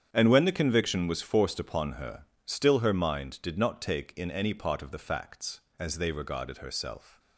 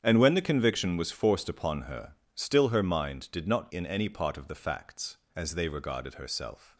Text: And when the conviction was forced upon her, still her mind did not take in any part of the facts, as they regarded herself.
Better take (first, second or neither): first